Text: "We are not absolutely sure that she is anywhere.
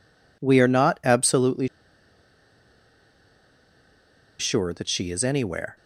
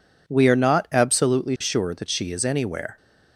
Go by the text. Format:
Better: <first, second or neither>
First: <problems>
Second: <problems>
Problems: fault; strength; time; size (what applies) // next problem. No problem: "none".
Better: second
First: pauses between "absolutely" and "sure"; strong; at 1.6 s; 2.7 s long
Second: none